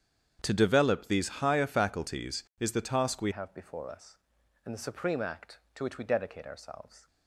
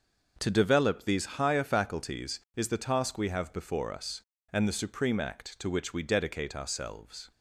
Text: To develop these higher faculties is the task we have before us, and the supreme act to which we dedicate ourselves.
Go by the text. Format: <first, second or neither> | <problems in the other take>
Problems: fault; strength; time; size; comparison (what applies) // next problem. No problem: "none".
second | starts louder than the rest; strong; until 1.4 s; 8.5 dB; noticeable in the second // changes voice at "have"; from 3.3 s on; 3.7 s long